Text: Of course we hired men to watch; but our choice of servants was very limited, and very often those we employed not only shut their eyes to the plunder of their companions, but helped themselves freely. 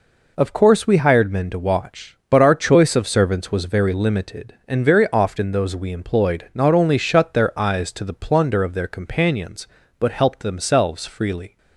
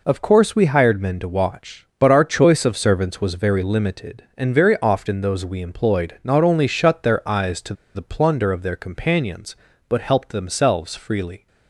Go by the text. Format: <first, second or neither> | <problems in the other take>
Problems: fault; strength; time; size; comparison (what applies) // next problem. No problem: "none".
first | pauses between "to" and "the"; slight; at 7.7 s; 0.21 s long